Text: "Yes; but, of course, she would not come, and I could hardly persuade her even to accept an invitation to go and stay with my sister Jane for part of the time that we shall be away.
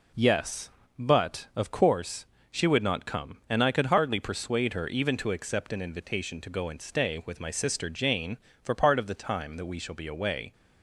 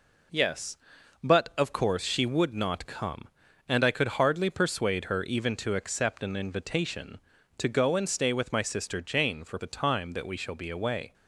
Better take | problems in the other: first | skips "part of"; at 9.5 s

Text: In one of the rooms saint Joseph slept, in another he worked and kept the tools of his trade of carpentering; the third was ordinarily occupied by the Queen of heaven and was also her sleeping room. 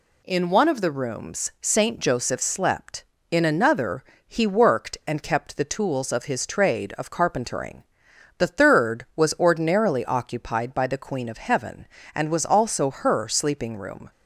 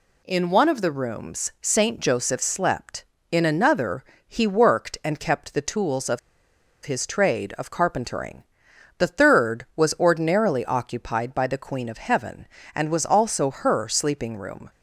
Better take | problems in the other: first | pauses between "another" and "he"; slight; at 4.0 s; 0.20 s long; slight in the first // pauses between "of" and "his"; noticeable; at 6.1 s; 0.64 s long

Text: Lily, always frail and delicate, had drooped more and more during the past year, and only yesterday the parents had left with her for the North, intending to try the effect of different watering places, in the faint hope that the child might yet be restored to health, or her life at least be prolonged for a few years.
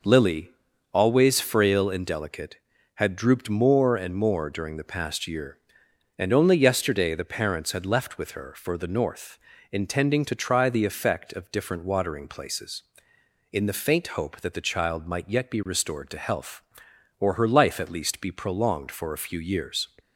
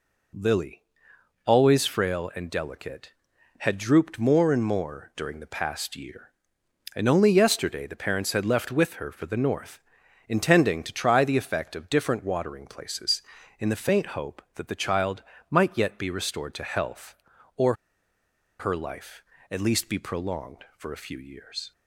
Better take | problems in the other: first | pauses between "child" and "might"; slight; at 15.2 s; 0.28 s long // pauses between "or" and "her"; noticeable; at 17.7 s; 0.85 s long

